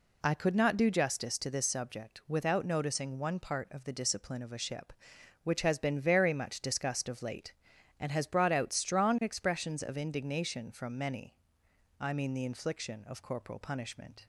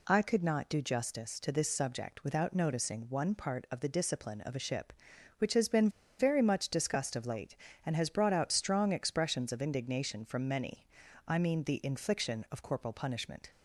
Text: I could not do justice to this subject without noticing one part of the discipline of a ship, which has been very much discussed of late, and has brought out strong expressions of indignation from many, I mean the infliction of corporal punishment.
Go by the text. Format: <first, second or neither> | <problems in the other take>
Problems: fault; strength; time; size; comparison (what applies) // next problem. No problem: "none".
first | pauses between "been" and "very"; slight; at 5.8 s; 0.30 s long